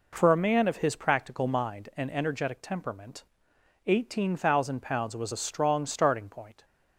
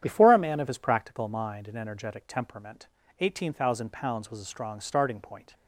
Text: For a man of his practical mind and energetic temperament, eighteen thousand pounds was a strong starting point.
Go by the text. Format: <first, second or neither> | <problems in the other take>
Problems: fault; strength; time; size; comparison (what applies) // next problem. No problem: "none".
first | starts louder than the rest; strong; until 1.0 s; 9.5 dB // says "Before" for "For"; at 0.0 s